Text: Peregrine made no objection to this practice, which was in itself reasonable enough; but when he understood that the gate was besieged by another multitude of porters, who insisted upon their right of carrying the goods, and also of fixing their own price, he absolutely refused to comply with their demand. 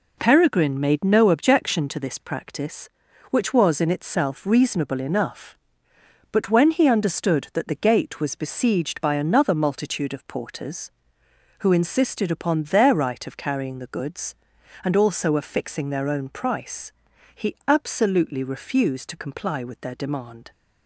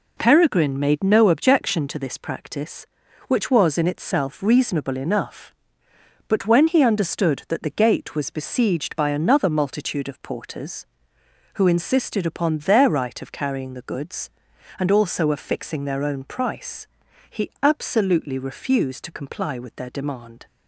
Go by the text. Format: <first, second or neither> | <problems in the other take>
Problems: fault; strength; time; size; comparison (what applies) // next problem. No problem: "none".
neither | none